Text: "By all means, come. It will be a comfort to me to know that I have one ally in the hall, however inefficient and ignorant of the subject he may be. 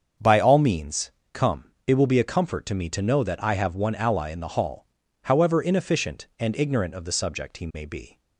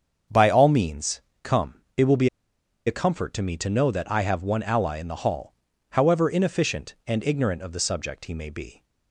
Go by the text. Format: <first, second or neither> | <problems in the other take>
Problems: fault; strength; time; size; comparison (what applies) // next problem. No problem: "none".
first | starts louder than the rest; until 1.5 s; 7 dB; also in the first // pauses between "be" and "a"; noticeable; at 2.2 s; 0.58 s long